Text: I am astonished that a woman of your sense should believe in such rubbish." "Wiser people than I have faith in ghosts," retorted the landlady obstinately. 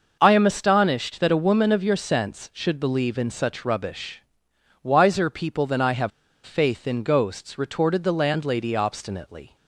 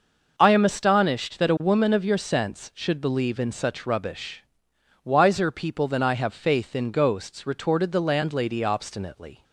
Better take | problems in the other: second | pauses between "have" and "faith"; slight; at 6.1 s; 0.34 s long

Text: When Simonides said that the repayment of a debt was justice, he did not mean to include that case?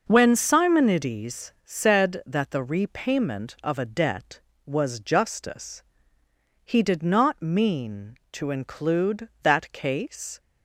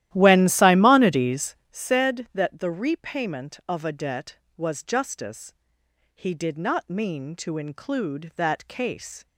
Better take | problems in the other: first | starts louder than the rest; strong; until 1.8 s; 13.5 dB // pauses between "Simonides" and "said"; slight; at 1.5 s; 0.16 s long

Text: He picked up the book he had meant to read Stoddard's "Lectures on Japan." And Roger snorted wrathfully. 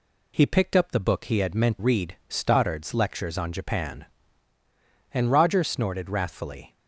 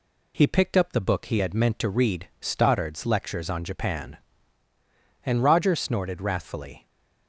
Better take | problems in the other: second | skips "to"; at 1.7 s

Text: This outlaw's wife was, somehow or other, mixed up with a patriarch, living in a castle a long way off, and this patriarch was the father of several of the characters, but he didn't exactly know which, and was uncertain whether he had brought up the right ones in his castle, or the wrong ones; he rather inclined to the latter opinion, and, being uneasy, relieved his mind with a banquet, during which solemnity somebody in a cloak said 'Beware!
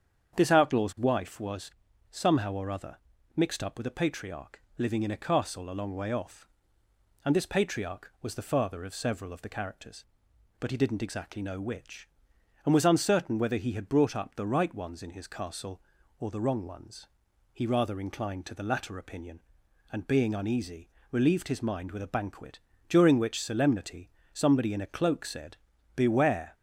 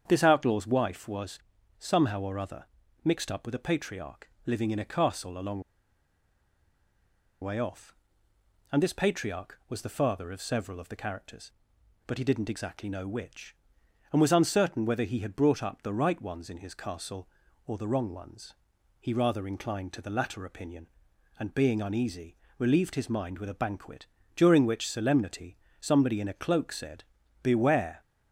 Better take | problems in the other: first | starts louder than the rest; strong; until 1.0 s; 8 dB; strong in the first // pauses between "long" and "way"; strong; at 5.6 s; 1.8 s long // pauses between "solemnity" and "somebody"; slight; at 25.5 s; 0.24 s long; slight in the first // pauses between "said" and "Beware"; at 27.0 s; 0.40 s long; also in the first

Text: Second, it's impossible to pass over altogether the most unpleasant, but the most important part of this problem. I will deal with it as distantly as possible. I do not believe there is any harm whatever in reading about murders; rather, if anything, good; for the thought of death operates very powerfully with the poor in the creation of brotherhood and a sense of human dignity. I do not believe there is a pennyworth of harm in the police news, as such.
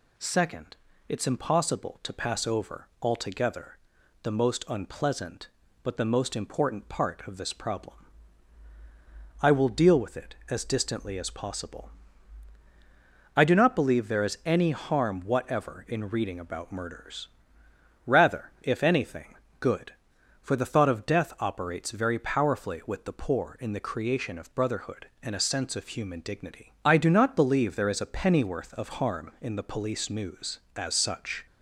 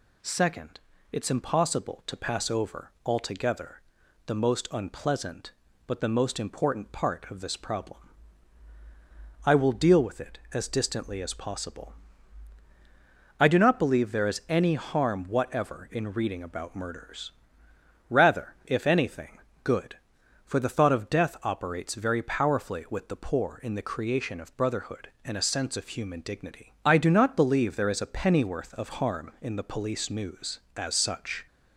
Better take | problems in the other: neither | pauses between "altogether" and "the"; the same in both

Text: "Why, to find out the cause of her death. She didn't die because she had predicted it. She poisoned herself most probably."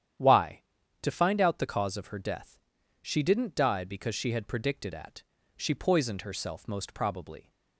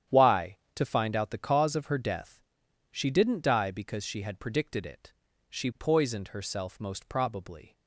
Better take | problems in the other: second | starts louder than the rest; strong; until 1.5 s; 10 dB; strong in the second // says "at" for "it"; at 4.9 s

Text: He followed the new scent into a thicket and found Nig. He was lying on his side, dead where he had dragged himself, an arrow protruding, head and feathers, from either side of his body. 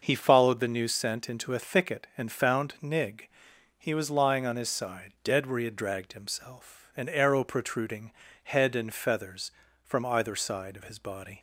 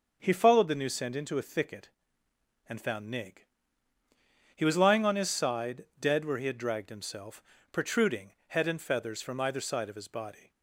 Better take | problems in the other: first | starts louder than the rest; until 1.2 s; 6.5 dB // skips "an arrow"; at 7.5 s

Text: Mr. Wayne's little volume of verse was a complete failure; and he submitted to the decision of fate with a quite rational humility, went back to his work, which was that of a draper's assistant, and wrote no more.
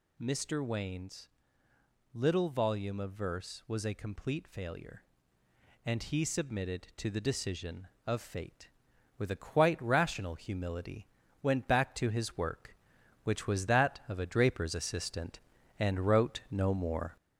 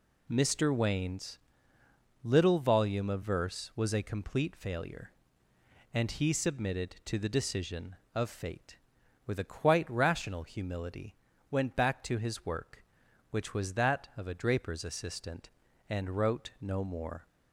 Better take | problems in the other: second | gets louder; throughout; 4 dB // pauses between "Wayne's" and "little"; noticeable; at 1.2 s; 0.82 s long; noticeable in the second

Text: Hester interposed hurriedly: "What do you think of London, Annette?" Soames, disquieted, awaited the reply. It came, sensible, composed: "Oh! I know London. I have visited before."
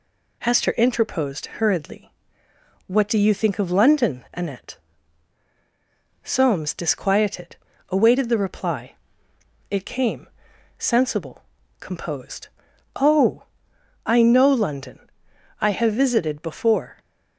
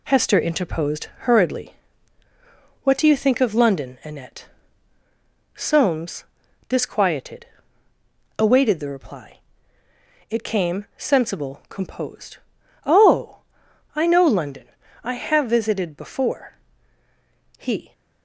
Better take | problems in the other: first | pauses between "interposed" and "hurriedly"; slight; at 1.0 s; 0.16 s long // goes on to say "He"; slight; from 17.5 s on; 0.34 s long

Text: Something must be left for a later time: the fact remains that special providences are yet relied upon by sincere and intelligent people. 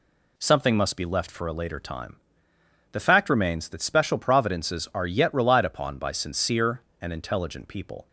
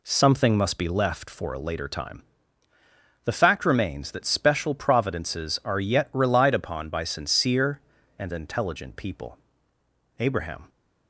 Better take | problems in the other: first | goes on to say "Abraham"; from 10.1 s on; 0.50 s long

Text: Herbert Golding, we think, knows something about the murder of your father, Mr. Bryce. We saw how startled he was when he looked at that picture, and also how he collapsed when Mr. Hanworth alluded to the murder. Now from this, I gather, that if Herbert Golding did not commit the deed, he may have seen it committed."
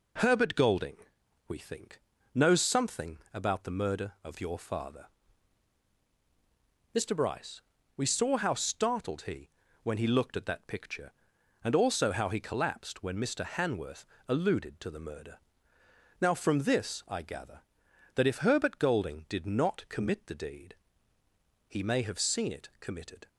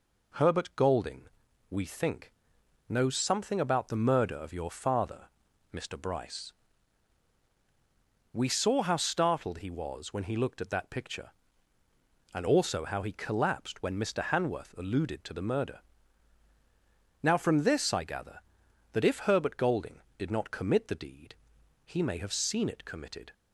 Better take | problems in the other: second | pauses between "something" and "about"; slight; at 3.1 s; 0.16 s long // skips "was"; at 9.6 s // pauses between "Hanworth" and "alluded"; slight; at 14.0 s; 0.20 s long

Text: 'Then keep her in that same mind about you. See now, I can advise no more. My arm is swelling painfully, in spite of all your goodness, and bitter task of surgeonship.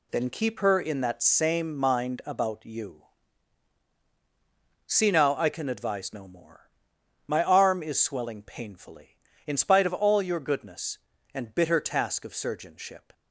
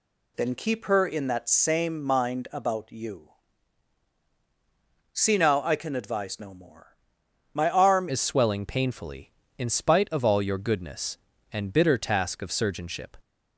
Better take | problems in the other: first | changes voice at "is"; from 8.0 s on; 5.1 s long

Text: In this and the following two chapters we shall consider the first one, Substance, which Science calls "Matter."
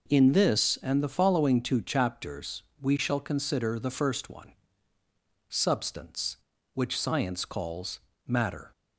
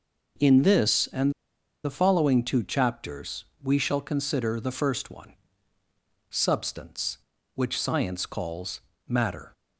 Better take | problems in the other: first | pauses between "and" and "the"; noticeable; at 1.3 s; 0.51 s long // pauses between "chapters" and "we"; slight; at 3.4 s; 0.18 s long; slight in the first // pauses between "calls" and "Matter"; slight; at 8.8 s; 0.26 s long; slight in the first

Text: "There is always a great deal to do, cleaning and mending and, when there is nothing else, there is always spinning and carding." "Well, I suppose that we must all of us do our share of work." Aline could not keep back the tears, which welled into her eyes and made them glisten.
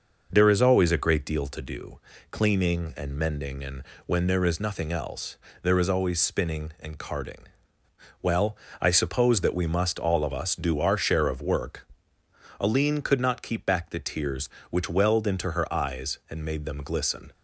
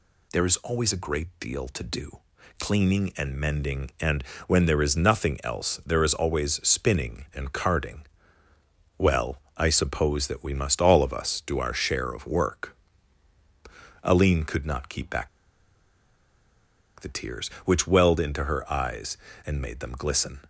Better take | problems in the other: first | pauses between "back" and "the"; strong; at 15.2 s; 1.7 s long

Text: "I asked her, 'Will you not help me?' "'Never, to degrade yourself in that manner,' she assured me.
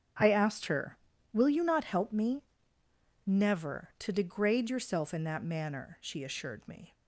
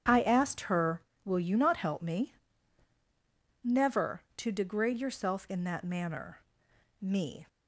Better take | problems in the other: first | starts louder than the rest; strong; until 1.3 s; 8.5 dB; strong in the first // skips "she assured"; at 6.7 s

